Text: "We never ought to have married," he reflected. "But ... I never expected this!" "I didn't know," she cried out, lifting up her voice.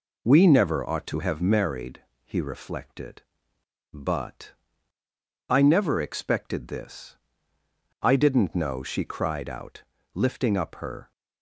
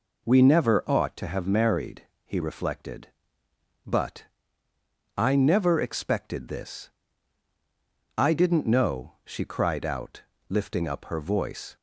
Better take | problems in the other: second | stops before "voice"; at 11.1 s

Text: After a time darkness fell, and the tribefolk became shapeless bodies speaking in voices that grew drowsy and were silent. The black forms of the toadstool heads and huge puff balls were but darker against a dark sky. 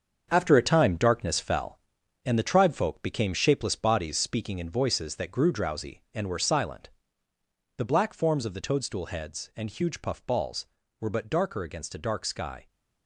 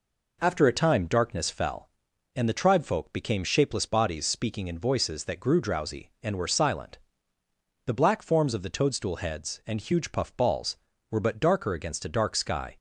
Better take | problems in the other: second | gets quieter; strong; throughout; 8 dB

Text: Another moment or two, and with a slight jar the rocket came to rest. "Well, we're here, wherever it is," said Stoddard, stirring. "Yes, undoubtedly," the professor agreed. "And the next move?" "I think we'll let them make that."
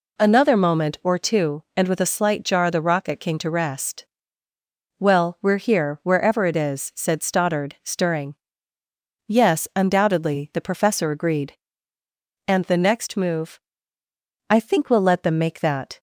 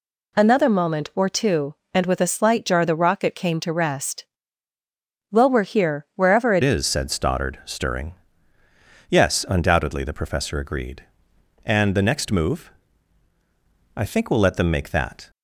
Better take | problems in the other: first | changes voice at "is"; from 6.6 s on; 8.6 s long

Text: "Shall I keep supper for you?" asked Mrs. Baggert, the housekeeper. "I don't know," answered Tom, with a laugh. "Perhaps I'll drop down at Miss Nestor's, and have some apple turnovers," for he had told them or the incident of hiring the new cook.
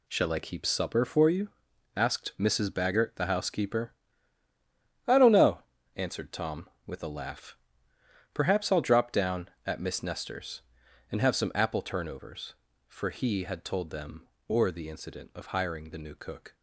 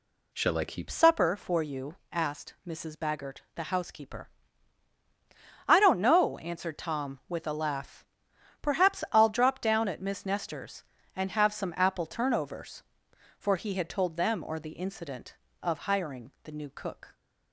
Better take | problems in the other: first | changes voice at "supper"; from 0.8 s on; 16.3 s long

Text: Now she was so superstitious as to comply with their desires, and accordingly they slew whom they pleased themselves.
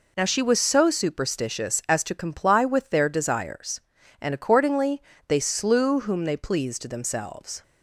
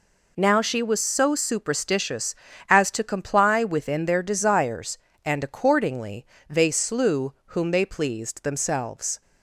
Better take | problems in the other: first | says "within" for "with"; at 3.6 s // pauses between "accordingly" and "they"; slight; at 6.2 s; 0.24 s long; slight in the first

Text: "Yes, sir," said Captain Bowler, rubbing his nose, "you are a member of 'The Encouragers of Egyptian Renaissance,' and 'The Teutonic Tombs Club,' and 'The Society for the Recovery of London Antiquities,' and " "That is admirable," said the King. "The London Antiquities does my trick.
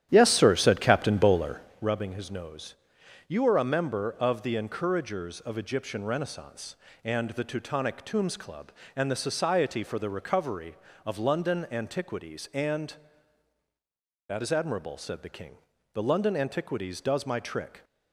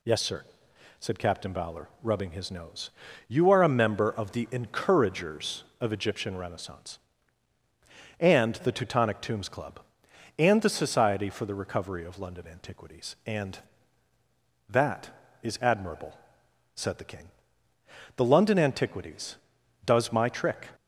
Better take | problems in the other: second | starts louder than the rest; strong; until 1.8 s; 11.5 dB

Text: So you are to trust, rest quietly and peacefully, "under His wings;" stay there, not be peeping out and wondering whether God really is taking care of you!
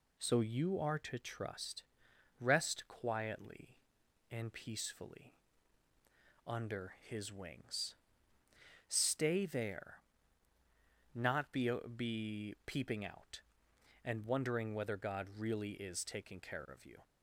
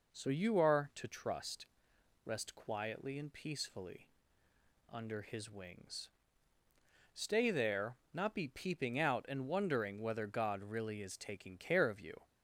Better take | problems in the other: second | says "be" twice; at 11.9 s

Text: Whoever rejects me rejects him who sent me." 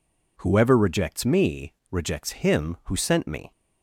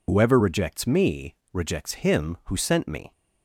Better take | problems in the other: first | loses the start of "Whoever"; at 0.0 s; 75 ms // pauses between "me" and "rejects"; slight; at 1.3 s; 0.18 s long; slight in the first

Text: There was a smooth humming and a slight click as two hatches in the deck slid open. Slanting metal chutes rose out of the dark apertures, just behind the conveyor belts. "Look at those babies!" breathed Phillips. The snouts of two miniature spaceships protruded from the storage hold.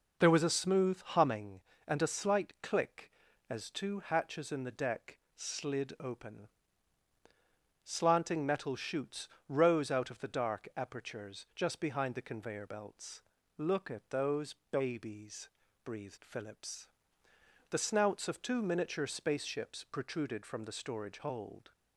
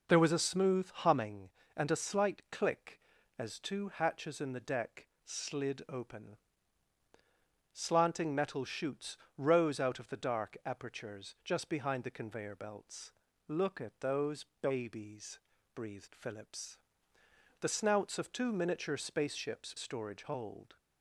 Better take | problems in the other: first | pauses between "deck" and "slid"; slight; at 5.0 s; 0.16 s long; slight in the first // pauses between "chutes" and "rose"; slight; at 9.1 s; 0.18 s long; slight in the first // pauses between "those" and "babies"; slight; at 14.4 s; 0.16 s long; slight in the first // skips "protruded from the"; at 19.7 s

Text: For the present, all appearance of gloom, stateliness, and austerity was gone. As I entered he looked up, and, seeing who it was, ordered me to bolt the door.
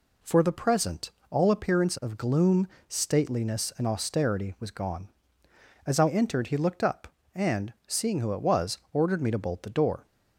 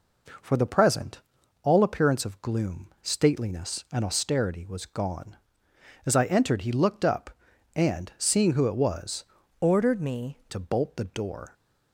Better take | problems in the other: first | changes voice from "ordered" to "me"; from 9.6 to 10.3 s; 0.7 s long

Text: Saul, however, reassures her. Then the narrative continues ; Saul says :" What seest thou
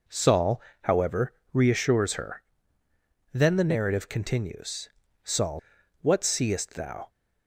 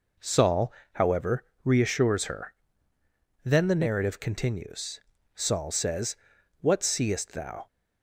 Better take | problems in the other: second | skips "says"; at 5.6 s

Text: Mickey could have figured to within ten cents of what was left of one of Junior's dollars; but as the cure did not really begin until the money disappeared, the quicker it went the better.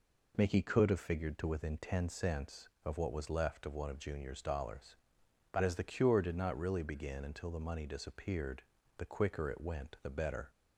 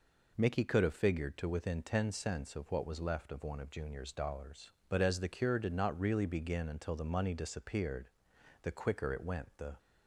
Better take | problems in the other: first | stops before "better"; at 9.7 s

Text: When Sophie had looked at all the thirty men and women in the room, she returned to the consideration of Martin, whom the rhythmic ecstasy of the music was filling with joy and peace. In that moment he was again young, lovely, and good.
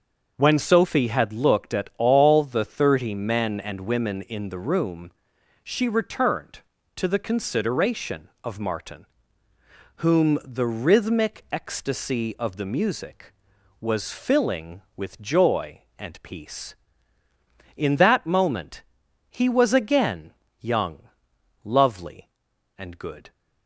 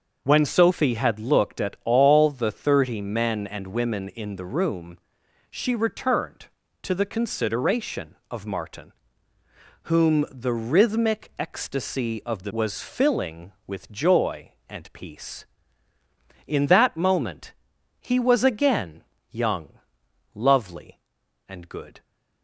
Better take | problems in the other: first | starts louder than the rest; until 1.2 s; 6.5 dB; also in the first // skips "music"; at 12.5 s // pauses between "moment" and "he"; noticeable; at 17.5 s; 0.46 s long; noticeable in the first // pauses between "again" and "young"; slight; at 19.0 s; 0.28 s long; slight in the first

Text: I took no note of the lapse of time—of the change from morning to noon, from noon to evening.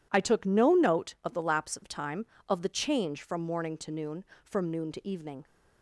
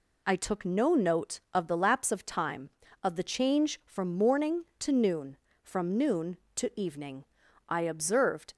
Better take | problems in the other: first | goes on to say "I observed"; noticeable; from 7.6 s on; 0.84 s long

